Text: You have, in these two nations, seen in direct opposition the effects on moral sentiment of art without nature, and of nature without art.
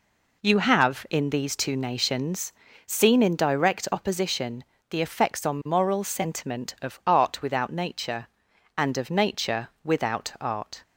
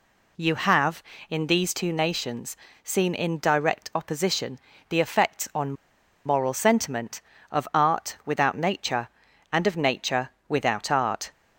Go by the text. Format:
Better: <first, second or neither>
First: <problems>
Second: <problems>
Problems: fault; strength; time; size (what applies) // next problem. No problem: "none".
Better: first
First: pauses between "opposition" and "the"; slight; at 4.6 s; 0.28 s long // pauses between "nature" and "without"; slight; at 9.6 s; 0.16 s long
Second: pauses between "opposition" and "the"; slight; at 4.5 s; 0.30 s long // pauses between "on" and "moral"; noticeable; at 5.7 s; 0.52 s long // pauses between "nature" and "without"; slight; at 10.3 s; 0.18 s long